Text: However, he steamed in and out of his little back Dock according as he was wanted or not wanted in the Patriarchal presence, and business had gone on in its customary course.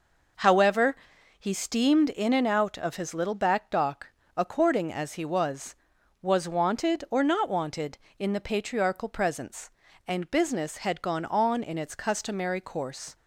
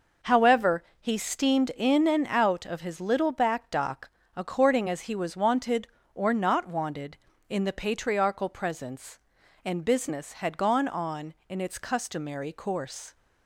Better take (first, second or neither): second